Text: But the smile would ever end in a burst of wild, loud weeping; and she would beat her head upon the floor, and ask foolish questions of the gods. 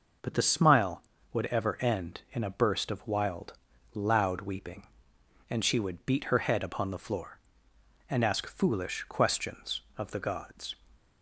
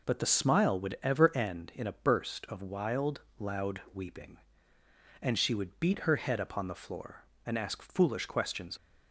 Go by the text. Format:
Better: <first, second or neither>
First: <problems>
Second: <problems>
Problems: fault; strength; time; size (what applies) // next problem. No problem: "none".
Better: first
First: none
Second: stops before "of the gods"; at 8.7 s